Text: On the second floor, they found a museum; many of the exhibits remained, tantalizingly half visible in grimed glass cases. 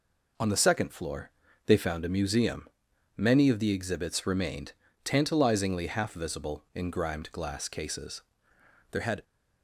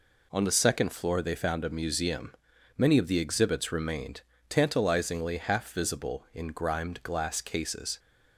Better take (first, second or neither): second